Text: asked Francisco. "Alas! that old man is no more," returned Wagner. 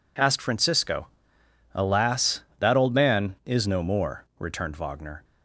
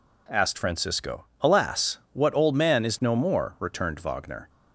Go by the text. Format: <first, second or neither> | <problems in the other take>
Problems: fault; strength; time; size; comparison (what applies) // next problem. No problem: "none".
first | says "what" for "that"; at 2.1 s